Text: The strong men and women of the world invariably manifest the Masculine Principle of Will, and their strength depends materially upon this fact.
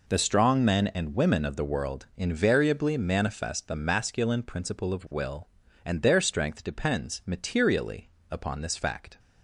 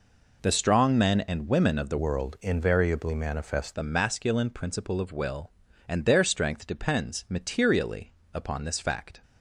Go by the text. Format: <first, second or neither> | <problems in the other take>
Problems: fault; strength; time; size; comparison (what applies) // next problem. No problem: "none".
first | changes voice from "world" to "manifest"; from 1.9 to 3.7 s; 1.8 s long // pauses between "materially" and "upon"; slight; at 8.1 s; 0.22 s long; slight in the first